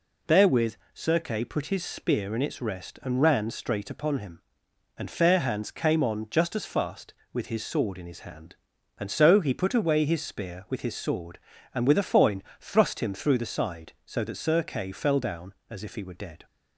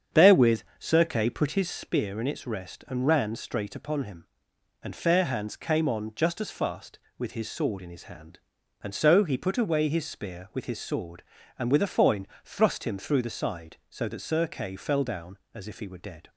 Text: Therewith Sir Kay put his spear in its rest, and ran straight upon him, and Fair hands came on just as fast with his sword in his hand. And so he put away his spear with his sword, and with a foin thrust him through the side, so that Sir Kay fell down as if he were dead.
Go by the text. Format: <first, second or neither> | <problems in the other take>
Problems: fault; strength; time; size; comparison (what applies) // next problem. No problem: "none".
first | starts louder than the rest; strong; until 1.8 s; 7.5 dB // pauses between "Therewith" and "Sir"; slight; at 0.6 s; 0.18 s long; slight in the first // pauses between "foin" and "thrust"; slight; at 12.2 s; 0.18 s long; slight in the first